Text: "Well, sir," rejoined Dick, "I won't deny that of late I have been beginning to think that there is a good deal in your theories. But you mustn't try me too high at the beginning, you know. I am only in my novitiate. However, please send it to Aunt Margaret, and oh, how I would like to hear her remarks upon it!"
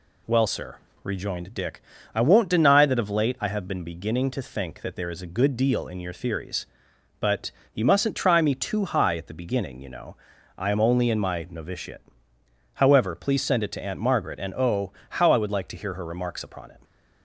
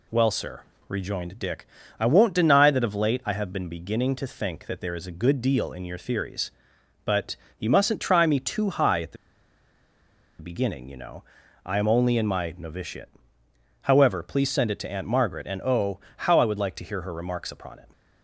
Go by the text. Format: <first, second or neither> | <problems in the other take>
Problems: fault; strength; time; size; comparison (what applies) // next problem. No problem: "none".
first | pauses between "But" and "you"; slight; at 7.3 s; 0.22 s long; slight in the first // pauses between "the" and "beginning"; at 9.1 s; 1.2 s long